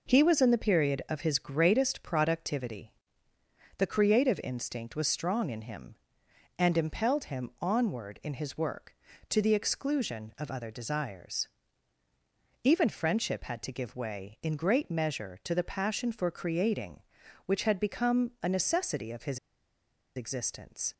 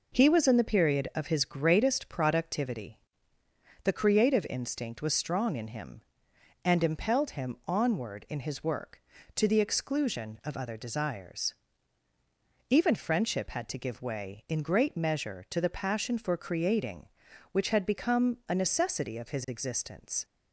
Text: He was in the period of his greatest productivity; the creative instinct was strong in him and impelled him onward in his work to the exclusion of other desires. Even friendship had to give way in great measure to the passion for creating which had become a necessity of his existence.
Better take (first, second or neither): second